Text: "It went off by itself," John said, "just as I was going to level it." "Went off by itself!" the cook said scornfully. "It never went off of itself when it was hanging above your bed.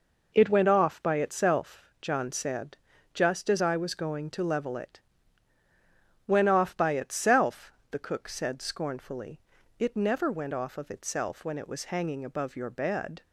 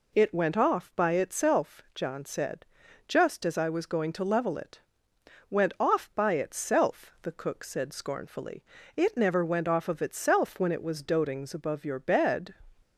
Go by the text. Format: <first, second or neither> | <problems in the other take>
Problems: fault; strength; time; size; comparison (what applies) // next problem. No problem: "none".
first | says "dotings" for "hanging"; at 11.0 s